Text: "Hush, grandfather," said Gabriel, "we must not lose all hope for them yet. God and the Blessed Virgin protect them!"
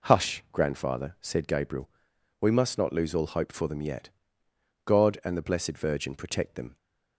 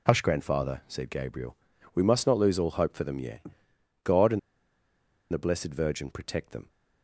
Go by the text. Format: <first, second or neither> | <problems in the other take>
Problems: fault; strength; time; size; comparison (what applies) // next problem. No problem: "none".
first | pauses between "and" and "the"; noticeable; at 4.3 s; 0.92 s long